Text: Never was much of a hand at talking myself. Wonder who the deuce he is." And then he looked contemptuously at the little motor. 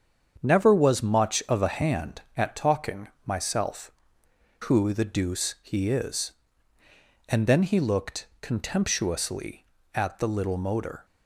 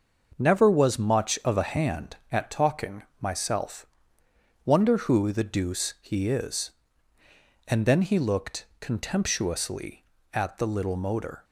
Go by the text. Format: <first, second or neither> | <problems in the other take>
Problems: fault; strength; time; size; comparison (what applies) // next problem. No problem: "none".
second | starts louder than the rest; strong; until 1.4 s; 7.5 dB; also in the second // pauses between "talking" and "myself"; slight; at 3.0 s; 0.18 s long; slight in the second // skips "Wonder"; at 4.2 s